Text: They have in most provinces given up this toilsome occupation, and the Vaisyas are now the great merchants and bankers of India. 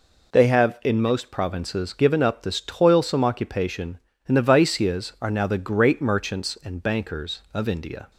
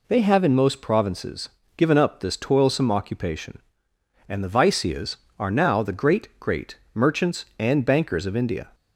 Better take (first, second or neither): first